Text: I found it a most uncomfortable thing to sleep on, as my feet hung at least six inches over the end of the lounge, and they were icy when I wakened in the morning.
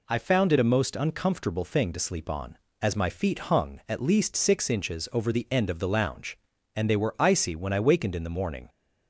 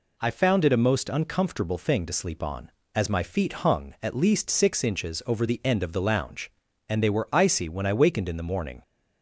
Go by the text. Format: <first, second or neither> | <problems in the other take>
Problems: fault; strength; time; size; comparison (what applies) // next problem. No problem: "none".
neither | none